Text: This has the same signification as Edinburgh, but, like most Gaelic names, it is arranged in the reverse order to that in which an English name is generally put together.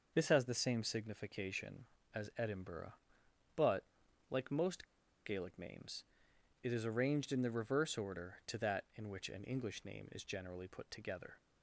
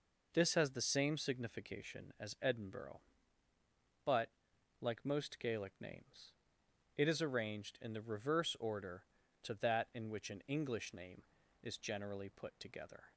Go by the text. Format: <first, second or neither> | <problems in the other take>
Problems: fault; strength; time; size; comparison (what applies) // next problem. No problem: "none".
second | starts louder than the rest; noticeable; until 1.1 s; 6 dB // pauses between "most" and "Gaelic"; at 4.8 s; 0.40 s long